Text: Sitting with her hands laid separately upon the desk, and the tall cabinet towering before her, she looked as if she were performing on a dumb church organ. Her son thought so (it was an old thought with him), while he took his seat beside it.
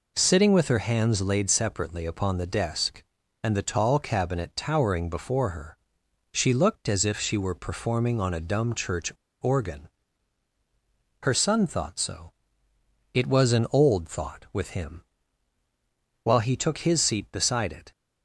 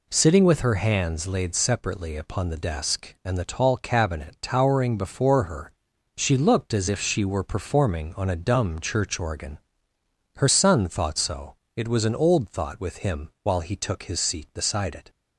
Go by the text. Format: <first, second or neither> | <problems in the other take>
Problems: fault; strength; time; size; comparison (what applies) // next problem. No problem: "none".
second | pauses between "church" and "organ"; slight; at 9.1 s; 0.29 s long